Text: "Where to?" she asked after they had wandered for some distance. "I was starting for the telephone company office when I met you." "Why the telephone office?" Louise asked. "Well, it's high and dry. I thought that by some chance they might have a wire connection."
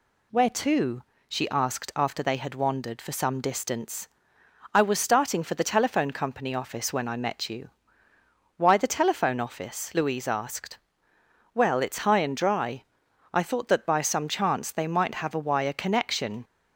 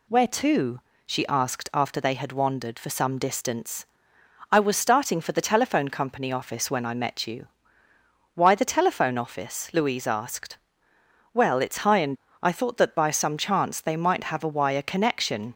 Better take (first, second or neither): first